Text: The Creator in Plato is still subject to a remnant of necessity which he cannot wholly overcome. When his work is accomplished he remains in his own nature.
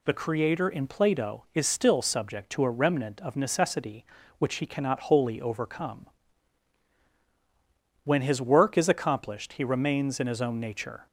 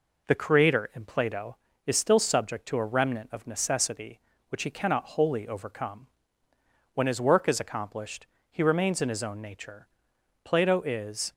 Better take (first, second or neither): first